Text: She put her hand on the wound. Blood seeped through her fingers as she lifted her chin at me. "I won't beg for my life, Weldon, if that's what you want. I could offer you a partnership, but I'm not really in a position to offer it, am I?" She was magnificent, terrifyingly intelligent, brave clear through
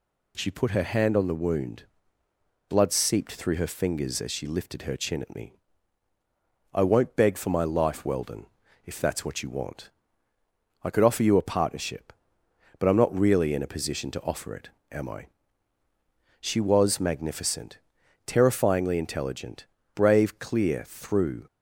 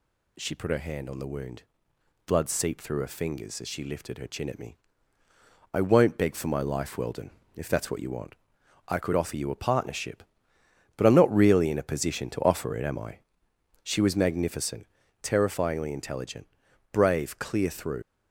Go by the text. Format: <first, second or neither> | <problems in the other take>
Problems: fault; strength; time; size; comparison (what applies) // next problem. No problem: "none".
first | leaves "through" unfinished; at 18.0 s; 90 ms